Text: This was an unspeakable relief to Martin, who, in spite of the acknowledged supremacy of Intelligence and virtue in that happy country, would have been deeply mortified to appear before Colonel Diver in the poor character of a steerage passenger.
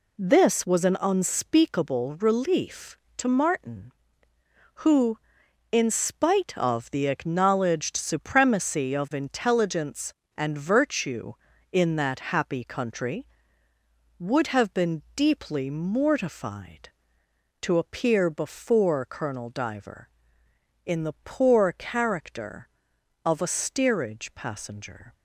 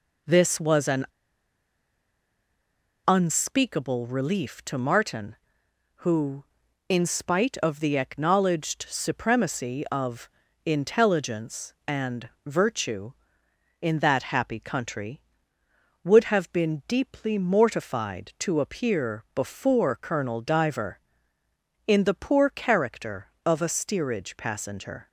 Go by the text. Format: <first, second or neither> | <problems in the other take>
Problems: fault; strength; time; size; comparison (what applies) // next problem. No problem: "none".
first | pauses between "an" and "unspeakable"; strong; at 1.0 s; 2.0 s long // pauses between "of" and "Intelligence"; at 10.2 s; 0.38 s long // pauses between "and" and "virtue"; slight; at 12.2 s; 0.16 s long